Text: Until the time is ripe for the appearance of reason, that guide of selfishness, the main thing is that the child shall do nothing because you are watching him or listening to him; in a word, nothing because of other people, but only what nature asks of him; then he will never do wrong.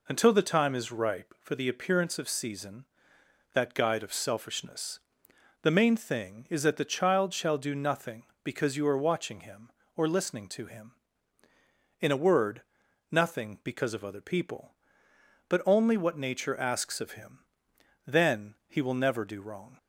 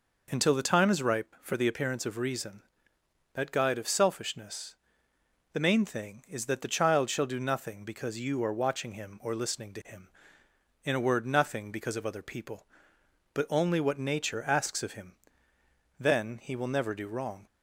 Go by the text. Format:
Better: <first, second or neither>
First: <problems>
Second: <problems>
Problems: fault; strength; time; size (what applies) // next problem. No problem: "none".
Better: second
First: says "season" for "reason"; at 2.2 s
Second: none